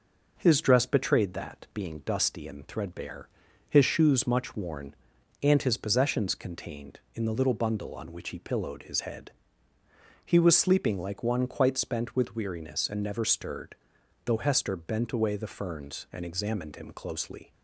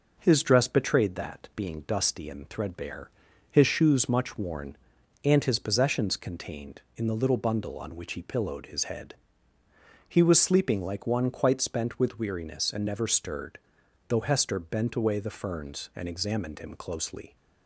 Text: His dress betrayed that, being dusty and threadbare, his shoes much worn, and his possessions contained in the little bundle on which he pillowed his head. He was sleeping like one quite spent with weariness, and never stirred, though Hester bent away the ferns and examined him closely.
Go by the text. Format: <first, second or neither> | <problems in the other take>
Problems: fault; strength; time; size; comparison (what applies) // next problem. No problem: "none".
neither | none